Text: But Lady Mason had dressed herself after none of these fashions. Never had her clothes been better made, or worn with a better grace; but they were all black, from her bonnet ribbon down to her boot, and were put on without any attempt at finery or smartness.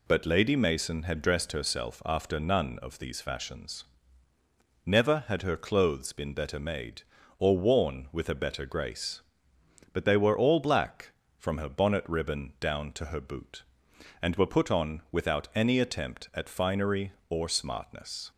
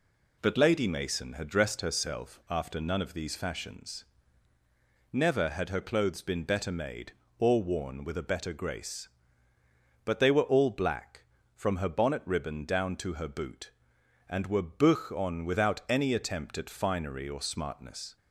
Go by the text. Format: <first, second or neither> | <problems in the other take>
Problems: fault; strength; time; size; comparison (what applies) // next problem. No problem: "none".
first | says "buch" for "put"; at 14.6 s